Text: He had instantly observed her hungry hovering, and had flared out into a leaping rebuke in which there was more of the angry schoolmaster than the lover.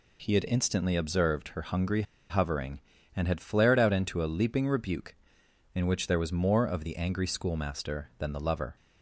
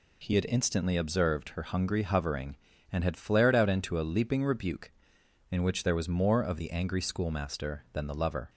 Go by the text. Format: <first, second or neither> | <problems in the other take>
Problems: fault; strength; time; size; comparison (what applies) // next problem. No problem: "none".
second | pauses between "hungry" and "hovering"; slight; at 2.0 s; 0.27 s long